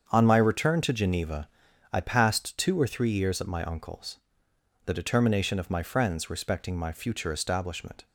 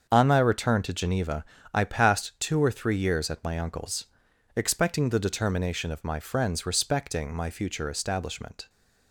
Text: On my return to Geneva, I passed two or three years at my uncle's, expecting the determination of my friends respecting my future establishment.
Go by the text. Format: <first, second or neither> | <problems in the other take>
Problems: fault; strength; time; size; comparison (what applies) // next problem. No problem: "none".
second | starts louder than the rest; strong; until 1.1 s; 7.5 dB; also in the second // skips "expecting"; at 4.5 s